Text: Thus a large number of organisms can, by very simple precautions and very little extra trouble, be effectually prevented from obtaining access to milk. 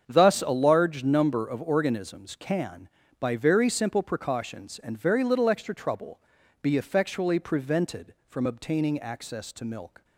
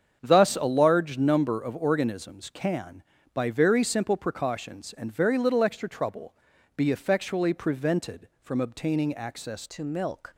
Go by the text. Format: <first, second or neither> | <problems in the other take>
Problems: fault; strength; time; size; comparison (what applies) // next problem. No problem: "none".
first | starts louder than the rest; strong; until 1.2 s; 7.5 dB; strong in the first // changes voice at "to"; from 9.7 s on; 0.6 s long